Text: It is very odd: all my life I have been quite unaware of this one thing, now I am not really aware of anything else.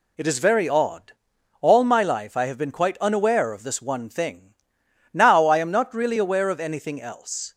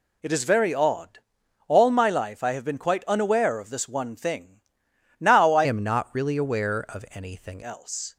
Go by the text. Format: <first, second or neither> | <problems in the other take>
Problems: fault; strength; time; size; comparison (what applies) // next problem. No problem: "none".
first | changes voice from "am" to "anything"; from 5.6 to 7.6 s; 2.0 s long